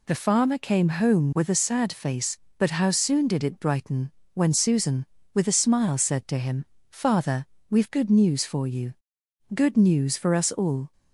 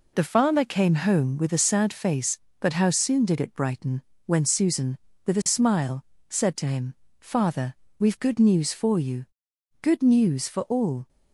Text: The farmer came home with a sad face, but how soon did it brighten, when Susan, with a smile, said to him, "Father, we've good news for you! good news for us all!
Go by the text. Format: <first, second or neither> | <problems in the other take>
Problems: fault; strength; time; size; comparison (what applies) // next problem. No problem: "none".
first | skips "us"; at 10.6 s